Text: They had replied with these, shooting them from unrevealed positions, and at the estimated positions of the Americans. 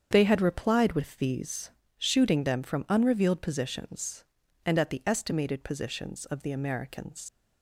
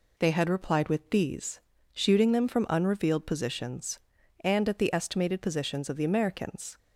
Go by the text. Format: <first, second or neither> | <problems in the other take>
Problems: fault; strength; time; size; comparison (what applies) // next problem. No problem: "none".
second | starts louder than the rest; strong; until 1.1 s; 7.5 dB // leaves "Americans" unfinished; at 7.2 s; 140 ms